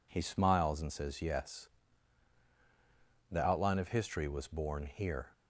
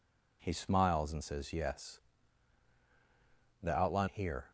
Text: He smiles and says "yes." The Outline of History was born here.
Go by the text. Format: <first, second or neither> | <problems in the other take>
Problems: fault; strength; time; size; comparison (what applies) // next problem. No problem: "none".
first | skips "of History was born"; at 4.0 s